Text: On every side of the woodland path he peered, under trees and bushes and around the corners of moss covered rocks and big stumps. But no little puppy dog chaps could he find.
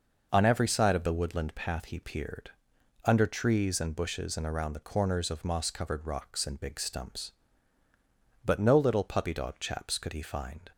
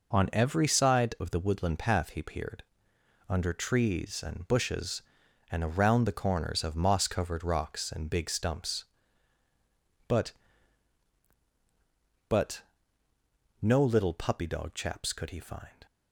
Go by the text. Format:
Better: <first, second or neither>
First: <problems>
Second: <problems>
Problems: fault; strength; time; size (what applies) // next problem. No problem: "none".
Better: first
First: none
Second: says "But" twice; at 12.2 s